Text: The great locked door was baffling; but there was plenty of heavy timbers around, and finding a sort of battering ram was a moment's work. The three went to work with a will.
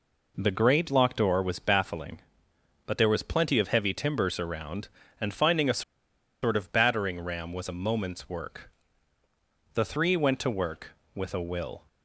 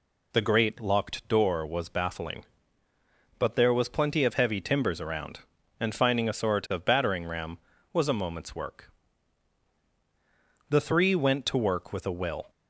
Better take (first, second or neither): second